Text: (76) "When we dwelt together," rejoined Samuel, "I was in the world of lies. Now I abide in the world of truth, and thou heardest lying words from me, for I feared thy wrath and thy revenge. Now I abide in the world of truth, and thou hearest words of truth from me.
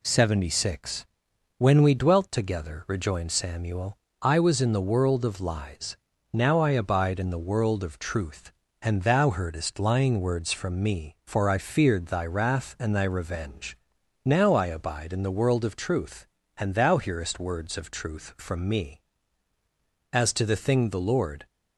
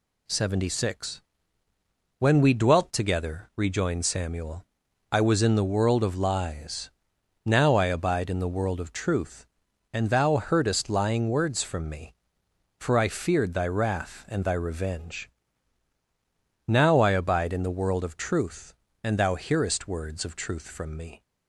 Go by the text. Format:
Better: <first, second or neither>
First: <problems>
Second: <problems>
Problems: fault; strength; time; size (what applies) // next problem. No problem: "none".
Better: second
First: goes on to say "As to the thing the Lord"; from 20.1 s on; 1.3 s long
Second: none